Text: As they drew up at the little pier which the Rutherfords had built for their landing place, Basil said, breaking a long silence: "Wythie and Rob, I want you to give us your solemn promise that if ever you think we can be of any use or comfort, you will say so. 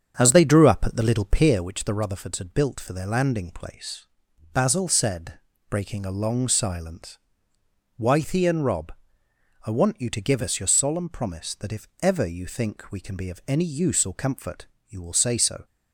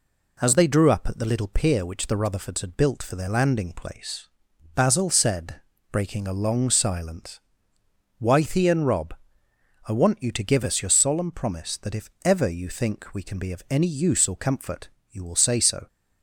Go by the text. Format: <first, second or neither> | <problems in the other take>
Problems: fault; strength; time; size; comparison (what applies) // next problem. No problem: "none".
second | starts louder than the rest; strong; until 1.8 s; 7.5 dB